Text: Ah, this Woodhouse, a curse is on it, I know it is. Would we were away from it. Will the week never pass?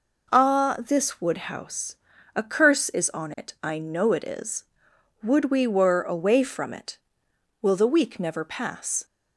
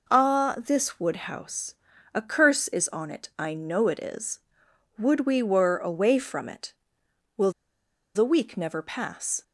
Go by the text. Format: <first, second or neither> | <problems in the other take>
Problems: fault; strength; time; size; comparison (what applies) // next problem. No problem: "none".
first | pauses between "Will" and "the"; noticeable; at 7.5 s; 0.64 s long